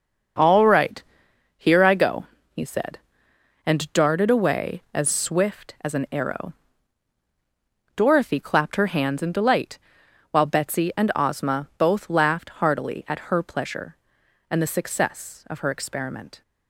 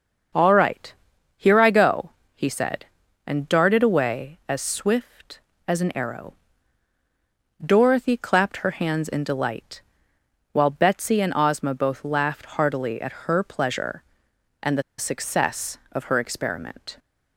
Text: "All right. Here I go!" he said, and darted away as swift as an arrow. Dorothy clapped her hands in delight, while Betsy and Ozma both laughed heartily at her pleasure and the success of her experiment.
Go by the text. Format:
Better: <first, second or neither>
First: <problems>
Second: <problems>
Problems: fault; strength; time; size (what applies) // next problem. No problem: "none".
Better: first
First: starts louder than the rest; until 1.9 s; 6.5 dB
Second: starts louder than the rest; until 1.7 s; 6.5 dB // pauses between "the" and "success"; slight; at 14.8 s; 0.16 s long